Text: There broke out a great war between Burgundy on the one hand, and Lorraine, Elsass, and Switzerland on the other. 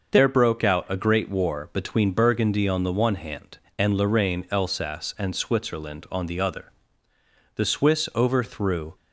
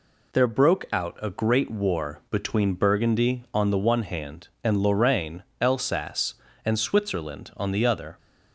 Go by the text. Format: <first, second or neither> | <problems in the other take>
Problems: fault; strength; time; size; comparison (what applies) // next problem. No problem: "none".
second | goes on to say "The Swiss overthrew"; from 7.5 s on; 1.4 s long